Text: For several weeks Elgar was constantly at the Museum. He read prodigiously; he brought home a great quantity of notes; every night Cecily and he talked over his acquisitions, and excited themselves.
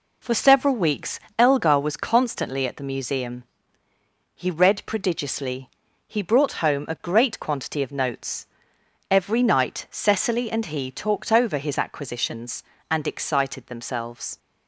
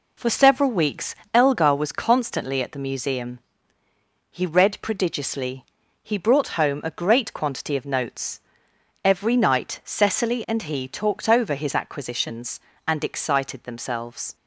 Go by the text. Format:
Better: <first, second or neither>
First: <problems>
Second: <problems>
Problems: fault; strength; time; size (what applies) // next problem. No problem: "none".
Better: neither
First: pauses between "weeks" and "Elgar"; slight; at 1.1 s; 0.18 s long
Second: pauses between "weeks" and "Elgar"; slight; at 1.1 s; 0.18 s long